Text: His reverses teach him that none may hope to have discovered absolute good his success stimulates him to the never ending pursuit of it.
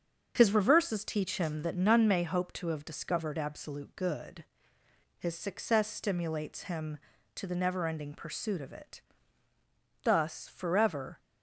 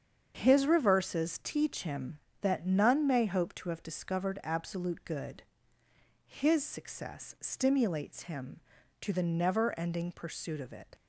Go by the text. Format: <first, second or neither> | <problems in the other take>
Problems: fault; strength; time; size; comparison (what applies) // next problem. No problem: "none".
second | starts louder than the rest; until 1.3 s; 7 dB; strong in the second // pauses between "good" and "his"; noticeable; at 4.4 s; 0.72 s long; noticeable in the second // goes on to say "Thus forever"; noticeable; from 10.0 s on; 1.1 s long